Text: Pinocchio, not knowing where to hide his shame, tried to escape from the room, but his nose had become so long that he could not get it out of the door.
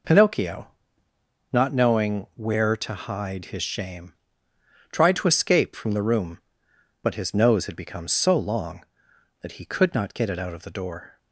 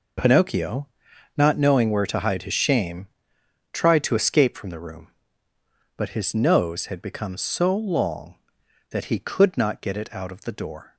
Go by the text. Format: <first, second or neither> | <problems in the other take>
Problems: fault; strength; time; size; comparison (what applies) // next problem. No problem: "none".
neither | none